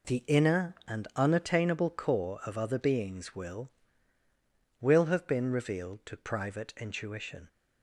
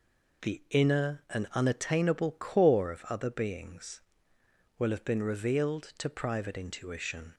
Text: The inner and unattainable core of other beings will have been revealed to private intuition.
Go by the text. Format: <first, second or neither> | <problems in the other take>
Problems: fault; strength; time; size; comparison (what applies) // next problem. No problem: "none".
second | says "will" twice; at 4.7 s